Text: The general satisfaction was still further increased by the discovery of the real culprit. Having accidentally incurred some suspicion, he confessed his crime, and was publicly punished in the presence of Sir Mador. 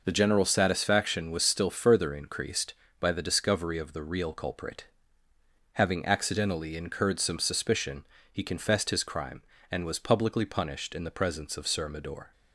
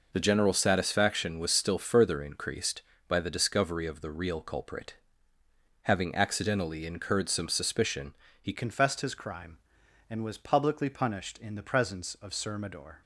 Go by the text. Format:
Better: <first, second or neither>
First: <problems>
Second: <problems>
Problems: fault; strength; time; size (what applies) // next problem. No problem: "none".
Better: first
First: none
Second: changes voice at "confessed"; from 8.5 s on; 4.5 s long